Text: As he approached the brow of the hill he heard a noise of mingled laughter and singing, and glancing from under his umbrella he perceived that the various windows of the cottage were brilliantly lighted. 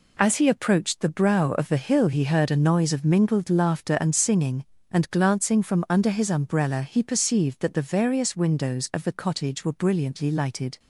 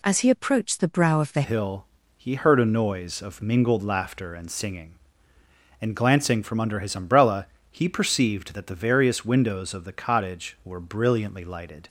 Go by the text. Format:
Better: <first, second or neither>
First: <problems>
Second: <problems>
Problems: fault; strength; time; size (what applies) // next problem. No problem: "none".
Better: first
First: none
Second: changes voice at "hill"; from 1.4 s on; 10.4 s long // pauses between "hill" and "he"; slight; at 1.8 s; 0.32 s long // pauses between "umbrella" and "he"; slight; at 7.4 s; 0.26 s long